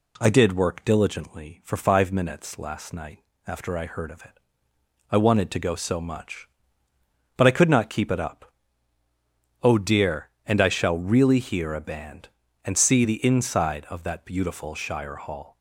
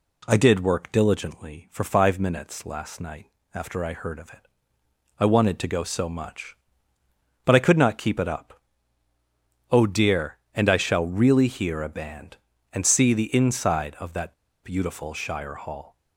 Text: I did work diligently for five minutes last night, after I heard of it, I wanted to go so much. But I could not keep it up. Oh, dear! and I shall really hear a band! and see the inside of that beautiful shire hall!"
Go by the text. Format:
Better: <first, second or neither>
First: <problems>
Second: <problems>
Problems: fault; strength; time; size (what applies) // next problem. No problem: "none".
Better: first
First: none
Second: pauses between "that" and "beautiful"; slight; at 14.3 s; 0.29 s long